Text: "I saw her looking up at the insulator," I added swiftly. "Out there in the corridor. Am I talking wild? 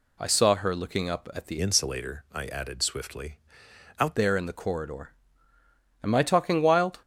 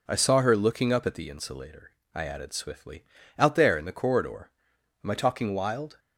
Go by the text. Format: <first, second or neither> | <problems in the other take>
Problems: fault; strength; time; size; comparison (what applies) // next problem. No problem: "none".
second | changes voice from "insulator" to "Out"; from 1.6 to 4.1 s; 2.5 s long